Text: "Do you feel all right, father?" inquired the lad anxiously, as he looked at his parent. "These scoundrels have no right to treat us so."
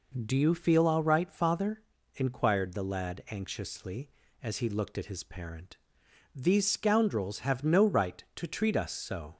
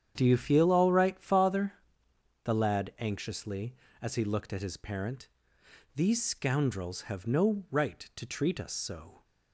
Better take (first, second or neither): first